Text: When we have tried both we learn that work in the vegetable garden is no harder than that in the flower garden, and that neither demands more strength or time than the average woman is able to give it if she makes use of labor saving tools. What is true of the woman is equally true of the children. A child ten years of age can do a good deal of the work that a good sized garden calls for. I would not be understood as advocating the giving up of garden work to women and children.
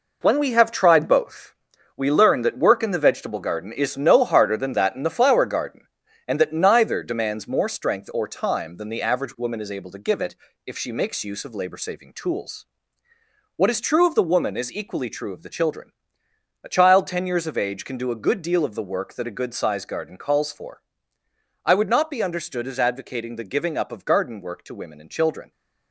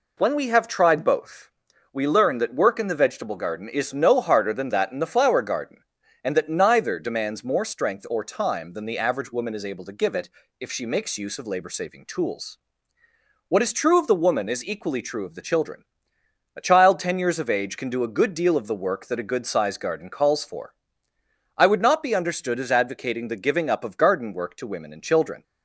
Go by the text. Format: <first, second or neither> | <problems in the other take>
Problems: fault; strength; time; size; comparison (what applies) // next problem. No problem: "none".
second | gets quieter; strong; throughout; 8 dB // pauses between "both" and "we"; at 1.5 s; 0.44 s long; also in the second // pauses between "it" and "if"; slight; at 10.3 s; 0.32 s long; slight in the second